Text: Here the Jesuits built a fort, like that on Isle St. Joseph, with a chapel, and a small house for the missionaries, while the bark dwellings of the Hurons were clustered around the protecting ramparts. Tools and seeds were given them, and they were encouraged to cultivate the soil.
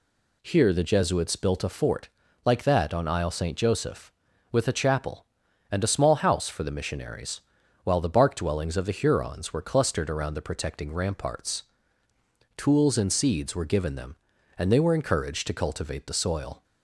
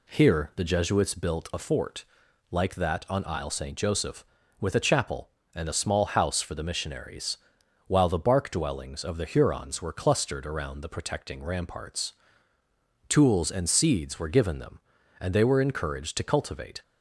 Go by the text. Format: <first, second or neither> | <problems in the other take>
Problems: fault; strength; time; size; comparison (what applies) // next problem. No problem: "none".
first | stops before "the soil"; at 16.8 s